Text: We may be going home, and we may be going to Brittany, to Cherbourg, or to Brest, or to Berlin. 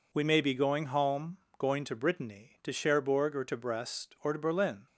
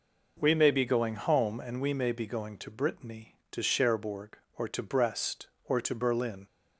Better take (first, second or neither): second